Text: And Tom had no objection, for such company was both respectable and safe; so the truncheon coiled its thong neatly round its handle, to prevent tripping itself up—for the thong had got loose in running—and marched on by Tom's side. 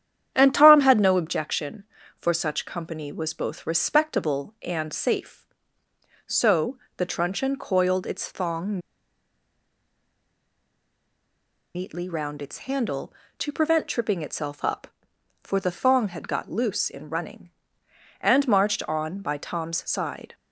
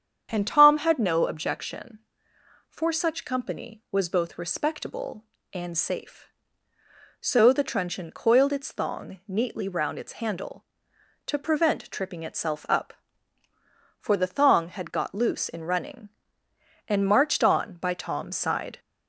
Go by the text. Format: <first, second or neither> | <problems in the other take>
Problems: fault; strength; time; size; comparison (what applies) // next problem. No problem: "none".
second | starts louder than the rest; strong; until 1.3 s; 9.5 dB; strong in the second // pauses between "so" and "the"; slight; at 6.7 s; 0.22 s long // pauses between "thong" and "neatly"; strong; at 8.7 s; 2.9 s long